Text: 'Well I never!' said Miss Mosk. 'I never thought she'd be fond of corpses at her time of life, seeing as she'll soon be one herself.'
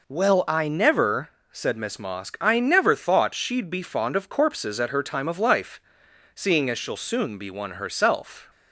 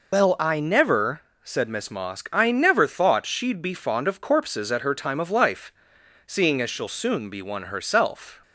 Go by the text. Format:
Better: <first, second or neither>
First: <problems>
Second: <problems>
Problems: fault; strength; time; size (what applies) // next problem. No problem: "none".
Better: first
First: none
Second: loses the start of "Well"; at 0.1 s; 150 ms